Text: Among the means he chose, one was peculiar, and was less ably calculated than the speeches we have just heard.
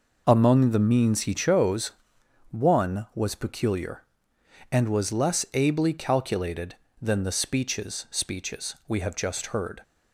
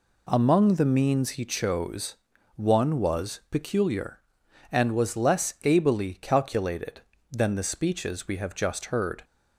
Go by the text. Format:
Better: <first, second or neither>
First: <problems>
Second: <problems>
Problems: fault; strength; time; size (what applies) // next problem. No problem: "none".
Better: second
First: says "speeches" twice; at 8.0 s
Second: none